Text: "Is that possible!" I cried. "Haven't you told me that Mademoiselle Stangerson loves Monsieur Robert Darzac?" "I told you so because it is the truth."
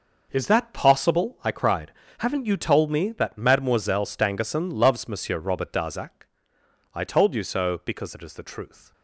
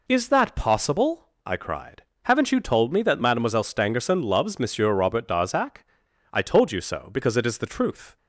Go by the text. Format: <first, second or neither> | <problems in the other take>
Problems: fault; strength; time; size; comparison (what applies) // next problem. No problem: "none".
second | gets quieter; strong; throughout; 11 dB